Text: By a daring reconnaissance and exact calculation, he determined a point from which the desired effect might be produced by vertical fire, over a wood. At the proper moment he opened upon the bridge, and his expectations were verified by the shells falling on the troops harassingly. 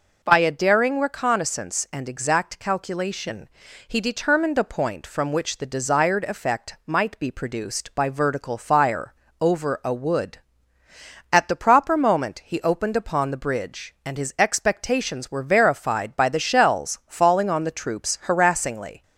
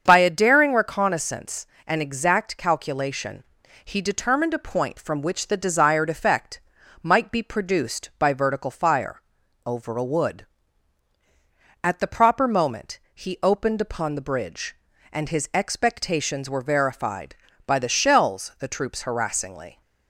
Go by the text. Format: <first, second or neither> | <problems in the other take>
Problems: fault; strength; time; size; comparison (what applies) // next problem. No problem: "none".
first | starts louder than the rest; strong; until 1.0 s; 7 dB // pauses between "effect" and "might"; at 6.6 s; 0.42 s long // pauses between "moment" and "he"; slight; at 13.0 s; 0.16 s long // skips "falling on"; at 18.5 s